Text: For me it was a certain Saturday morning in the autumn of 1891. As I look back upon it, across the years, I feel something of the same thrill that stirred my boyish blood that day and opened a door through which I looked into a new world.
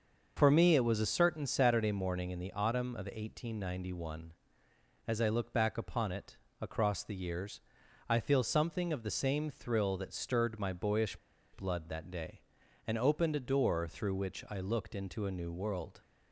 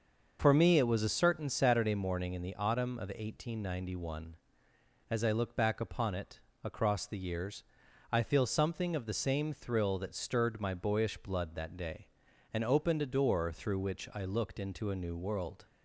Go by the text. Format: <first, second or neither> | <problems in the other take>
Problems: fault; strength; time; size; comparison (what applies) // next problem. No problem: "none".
second | starts louder than the rest; until 1.3 s; 6 dB; also in the second // pauses between "boyish" and "blood"; at 11.1 s; 0.37 s long